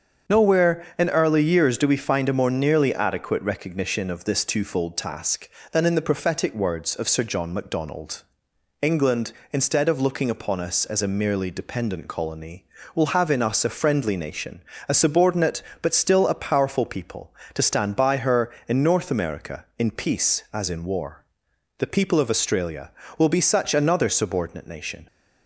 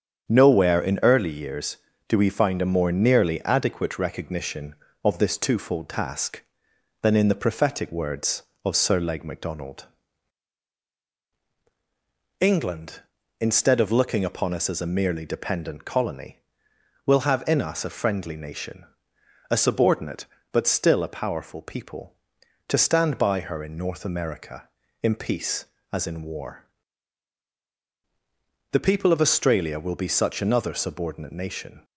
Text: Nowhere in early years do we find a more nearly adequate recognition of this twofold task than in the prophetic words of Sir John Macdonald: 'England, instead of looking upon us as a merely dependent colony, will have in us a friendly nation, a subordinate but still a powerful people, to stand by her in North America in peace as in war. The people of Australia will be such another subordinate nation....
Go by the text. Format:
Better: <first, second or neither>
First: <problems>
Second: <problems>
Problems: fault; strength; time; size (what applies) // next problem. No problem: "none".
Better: first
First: starts louder than the rest; until 1.4 s; 7 dB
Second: starts louder than the rest; strong; until 1.3 s; 8 dB // says "Leg" for "John"; at 8.9 s